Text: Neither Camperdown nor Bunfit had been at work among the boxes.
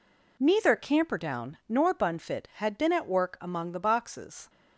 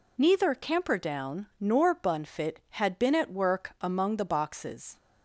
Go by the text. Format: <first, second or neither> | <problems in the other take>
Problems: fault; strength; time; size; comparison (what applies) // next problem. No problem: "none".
neither | none